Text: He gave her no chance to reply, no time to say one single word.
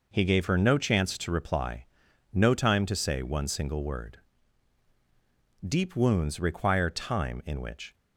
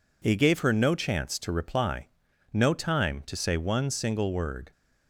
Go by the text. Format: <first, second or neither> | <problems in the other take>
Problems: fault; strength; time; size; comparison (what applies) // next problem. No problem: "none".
second | goes on to say "Deep wounds require time in which"; strong; from 5.6 s on; 2.2 s long